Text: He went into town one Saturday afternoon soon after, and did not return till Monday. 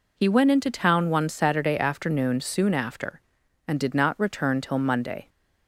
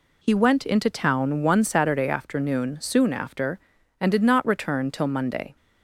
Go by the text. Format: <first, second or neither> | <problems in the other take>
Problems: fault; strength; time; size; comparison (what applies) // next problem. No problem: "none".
neither | none